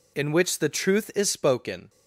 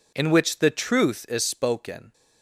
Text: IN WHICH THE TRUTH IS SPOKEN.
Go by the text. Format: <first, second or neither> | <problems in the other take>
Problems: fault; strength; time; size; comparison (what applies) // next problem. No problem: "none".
neither | none